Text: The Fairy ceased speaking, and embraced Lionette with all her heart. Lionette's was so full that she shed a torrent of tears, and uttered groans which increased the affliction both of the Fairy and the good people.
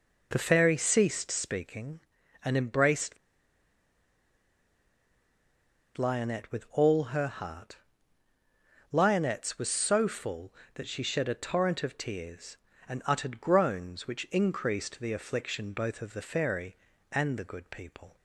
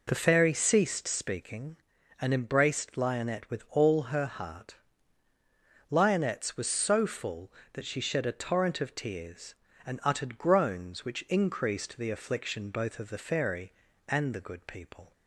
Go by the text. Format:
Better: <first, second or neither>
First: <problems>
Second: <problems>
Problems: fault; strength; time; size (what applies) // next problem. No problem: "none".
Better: second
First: pauses between "embraced" and "Lionette"; strong; at 3.1 s; 2.8 s long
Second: none